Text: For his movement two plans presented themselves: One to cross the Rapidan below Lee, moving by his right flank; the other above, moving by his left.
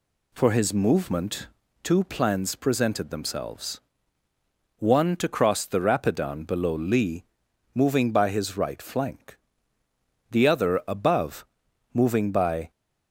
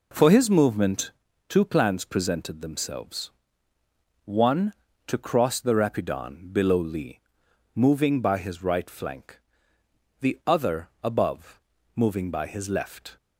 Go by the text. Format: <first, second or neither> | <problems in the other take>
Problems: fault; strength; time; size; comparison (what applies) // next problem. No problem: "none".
second | pauses between "movement" and "two"; slight; at 1.4 s; 0.36 s long; also in the second // stops before "his left"; at 12.6 s